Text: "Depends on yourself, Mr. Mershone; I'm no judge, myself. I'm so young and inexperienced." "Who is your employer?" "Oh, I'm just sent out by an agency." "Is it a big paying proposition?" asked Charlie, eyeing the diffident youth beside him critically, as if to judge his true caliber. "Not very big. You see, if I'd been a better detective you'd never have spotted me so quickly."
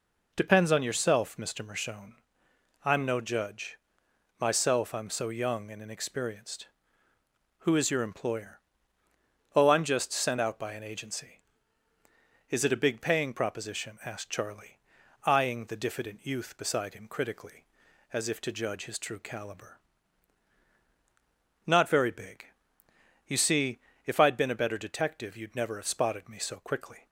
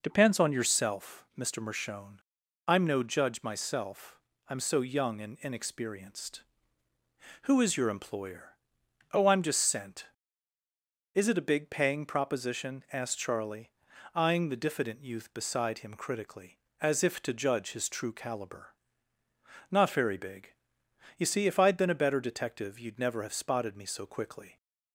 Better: first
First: none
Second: skips "out by an agency"; at 10.5 s

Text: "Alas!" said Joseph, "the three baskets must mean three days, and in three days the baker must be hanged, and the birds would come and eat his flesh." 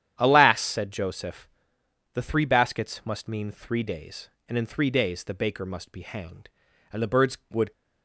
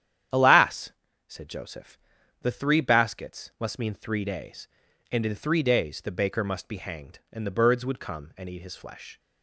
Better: second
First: starts louder than the rest; strong; until 1.1 s; 10 dB // stops before "come and eat his flesh"; at 7.7 s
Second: starts louder than the rest; strong; until 1.6 s; 10 dB

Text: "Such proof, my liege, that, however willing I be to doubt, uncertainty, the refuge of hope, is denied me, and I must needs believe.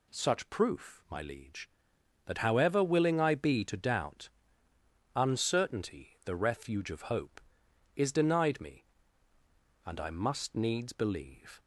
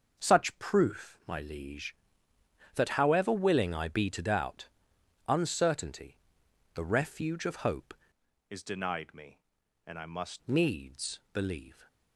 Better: first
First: none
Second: starts louder than the rest; until 1.2 s; 6 dB // changes voice from "is" to "must"; from 8.4 to 10.4 s; 2.0 s long

